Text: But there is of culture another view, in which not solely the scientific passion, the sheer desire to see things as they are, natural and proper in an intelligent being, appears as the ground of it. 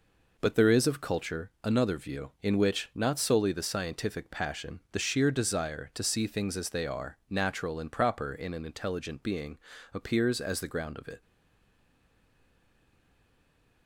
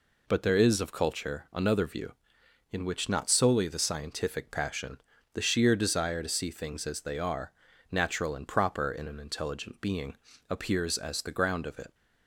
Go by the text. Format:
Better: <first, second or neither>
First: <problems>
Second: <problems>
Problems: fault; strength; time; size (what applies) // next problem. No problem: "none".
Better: second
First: stays silent after the last word; strong; from 11.2 s on; 2.6 s long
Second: none